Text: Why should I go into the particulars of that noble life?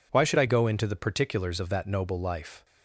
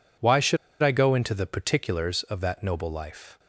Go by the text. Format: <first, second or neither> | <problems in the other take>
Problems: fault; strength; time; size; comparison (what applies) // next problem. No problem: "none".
first | pauses between "should" and "I"; slight; at 0.5 s; 0.25 s long